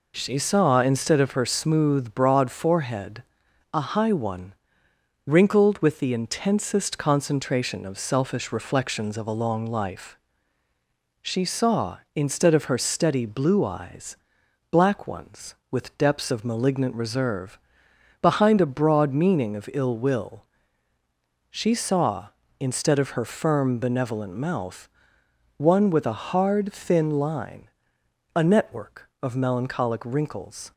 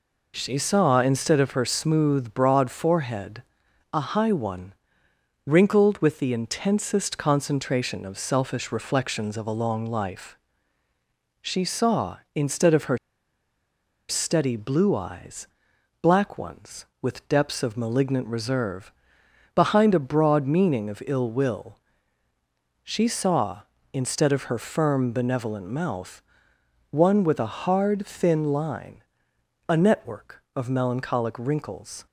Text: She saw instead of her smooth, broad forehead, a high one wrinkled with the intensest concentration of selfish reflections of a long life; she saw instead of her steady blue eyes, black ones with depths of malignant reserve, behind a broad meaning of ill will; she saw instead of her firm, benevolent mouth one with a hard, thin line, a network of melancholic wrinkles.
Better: first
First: pauses between "one" and "wrinkled"; noticeable; at 4.5 s; 0.74 s long // pauses between "mouth" and "one"; noticeable; at 24.9 s; 0.66 s long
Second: pauses between "one" and "wrinkled"; noticeable; at 4.7 s; 0.74 s long // pauses between "her" and "steady"; at 12.9 s; 1.1 s long // pauses between "mouth" and "one"; noticeable; at 26.2 s; 0.66 s long

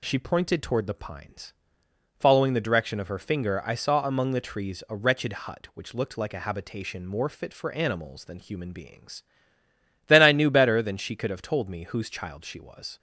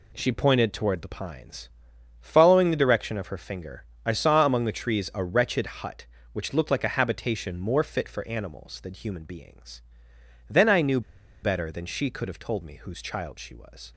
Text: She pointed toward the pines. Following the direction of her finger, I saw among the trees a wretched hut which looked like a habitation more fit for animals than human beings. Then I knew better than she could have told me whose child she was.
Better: first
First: none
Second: pauses between "knew" and "better"; at 11.0 s; 0.42 s long

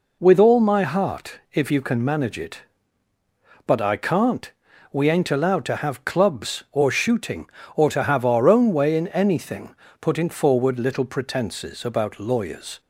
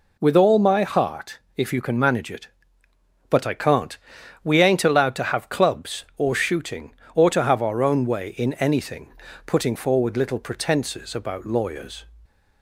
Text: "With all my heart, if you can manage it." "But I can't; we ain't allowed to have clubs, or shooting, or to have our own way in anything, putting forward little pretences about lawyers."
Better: neither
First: none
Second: none

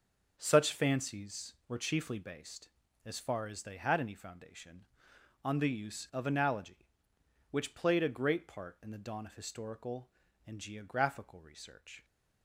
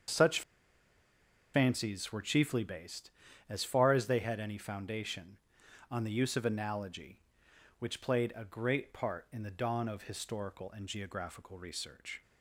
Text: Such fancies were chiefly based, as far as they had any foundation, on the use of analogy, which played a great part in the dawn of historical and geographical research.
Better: first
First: none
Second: starts louder than the rest; until 2.2 s; 7 dB // pauses between "Such" and "fancies"; at 0.4 s; 1.1 s long

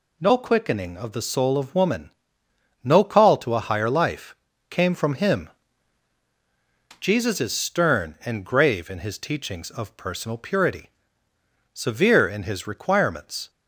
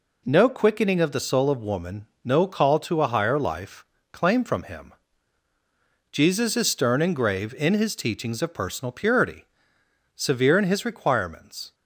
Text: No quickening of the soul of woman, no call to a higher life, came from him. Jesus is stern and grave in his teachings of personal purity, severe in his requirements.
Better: first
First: none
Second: says "claim" for "came"; at 4.1 s

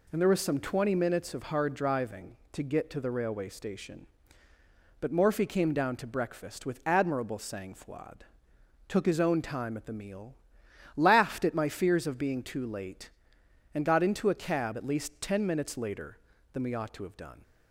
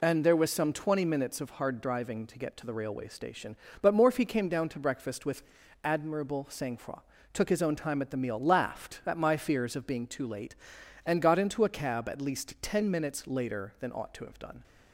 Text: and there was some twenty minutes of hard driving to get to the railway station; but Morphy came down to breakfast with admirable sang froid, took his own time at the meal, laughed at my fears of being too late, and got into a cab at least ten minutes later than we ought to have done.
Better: first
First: none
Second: pauses between "with" and "admirable"; at 5.4 s; 0.40 s long // skips "we"; at 13.9 s

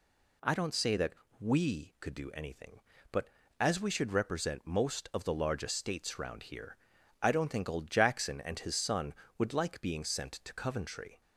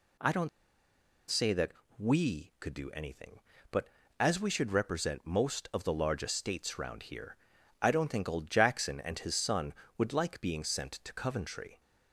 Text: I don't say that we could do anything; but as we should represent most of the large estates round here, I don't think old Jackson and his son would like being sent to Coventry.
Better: first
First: pauses between "that" and "we"; slight; at 1.1 s; 0.26 s long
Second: pauses between "don't" and "say"; noticeable; at 0.4 s; 0.80 s long // pauses between "that" and "we"; slight; at 1.7 s; 0.26 s long

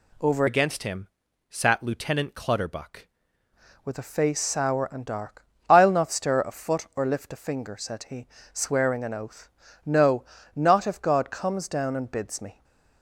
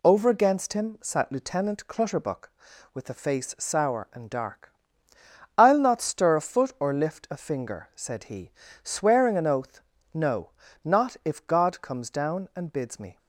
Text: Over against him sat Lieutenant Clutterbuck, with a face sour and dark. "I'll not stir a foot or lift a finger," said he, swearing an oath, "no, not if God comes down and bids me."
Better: second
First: changes voice from "against" to "Clutterbuck"; from 0.4 to 3.0 s; 2.6 s long // pauses between "him" and "sat"; at 1.0 s; 0.40 s long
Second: none

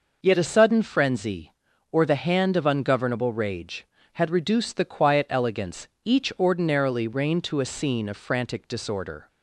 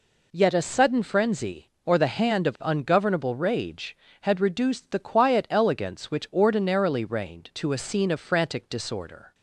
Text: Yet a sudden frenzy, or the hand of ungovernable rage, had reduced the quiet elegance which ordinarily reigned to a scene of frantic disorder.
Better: second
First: says "each" for "which"; at 6.0 s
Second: none

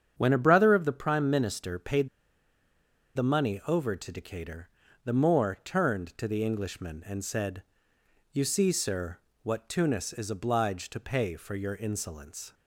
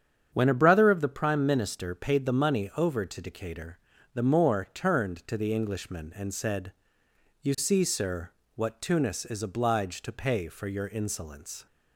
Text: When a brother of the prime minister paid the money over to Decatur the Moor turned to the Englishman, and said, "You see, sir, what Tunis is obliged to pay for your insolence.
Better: second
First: starts louder than the rest; strong; until 1.1 s; 8 dB // pauses between "paid" and "the"; at 2.0 s; 1.0 s long // pauses between "Decatur" and "the"; at 4.6 s; 0.38 s long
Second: starts louder than the rest; strong; until 1.3 s; 8 dB // pauses between "Decatur" and "the"; at 3.7 s; 0.38 s long

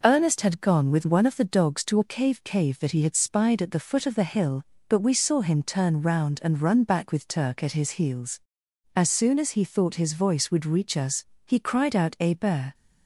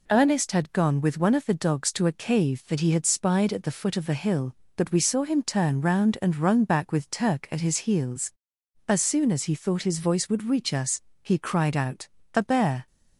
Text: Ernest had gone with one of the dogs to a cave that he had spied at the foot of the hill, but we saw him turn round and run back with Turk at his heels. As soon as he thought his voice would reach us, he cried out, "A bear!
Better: second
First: says "cave" twice; at 2.4 s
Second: none

